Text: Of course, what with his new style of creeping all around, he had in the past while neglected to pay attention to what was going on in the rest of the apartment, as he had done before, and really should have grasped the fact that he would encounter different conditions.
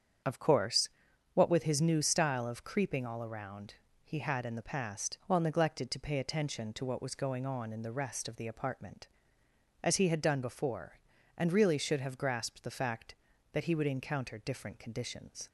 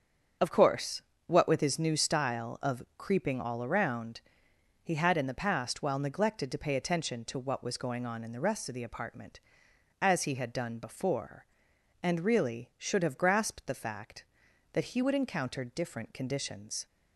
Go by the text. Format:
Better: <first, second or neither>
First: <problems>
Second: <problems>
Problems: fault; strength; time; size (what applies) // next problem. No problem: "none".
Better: neither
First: starts louder than the rest; strong; until 1.7 s; 8 dB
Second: starts louder than the rest; strong; until 1.6 s; 7 dB